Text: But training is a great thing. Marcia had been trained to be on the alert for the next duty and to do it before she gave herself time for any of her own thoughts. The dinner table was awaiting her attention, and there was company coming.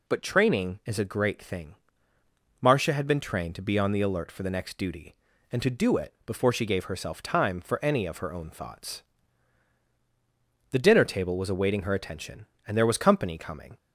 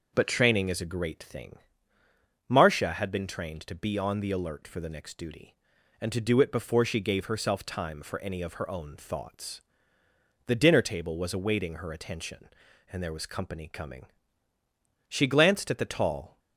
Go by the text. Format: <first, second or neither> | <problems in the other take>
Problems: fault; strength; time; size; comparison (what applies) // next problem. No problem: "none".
first | goes on to say "She glanced at the tall"; noticeable; from 15.0 s on; 1.3 s long